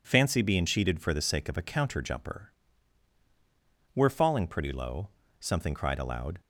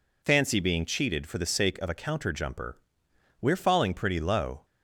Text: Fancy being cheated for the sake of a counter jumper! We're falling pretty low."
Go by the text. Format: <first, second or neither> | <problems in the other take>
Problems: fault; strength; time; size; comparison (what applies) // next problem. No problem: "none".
second | goes on to say "Something cried aloud"; noticeable; from 5.3 s on; 1.0 s long